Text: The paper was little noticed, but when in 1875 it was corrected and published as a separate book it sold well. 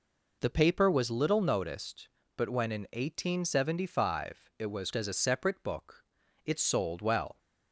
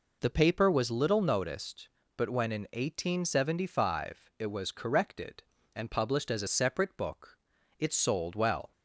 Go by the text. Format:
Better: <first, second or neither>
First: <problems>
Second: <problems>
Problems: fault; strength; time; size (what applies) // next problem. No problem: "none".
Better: second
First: skips "corrected and published"; at 4.9 s // pauses between "book" and "it"; at 6.0 s; 0.42 s long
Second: pauses between "book" and "it"; at 7.3 s; 0.42 s long